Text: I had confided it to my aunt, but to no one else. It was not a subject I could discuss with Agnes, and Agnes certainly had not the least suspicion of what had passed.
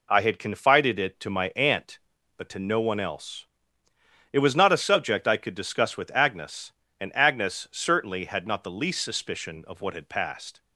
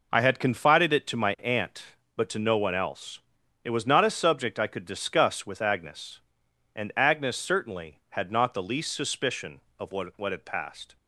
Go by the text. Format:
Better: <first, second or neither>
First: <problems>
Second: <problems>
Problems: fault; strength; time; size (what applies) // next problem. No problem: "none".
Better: first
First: none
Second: says "what" twice; at 10.1 s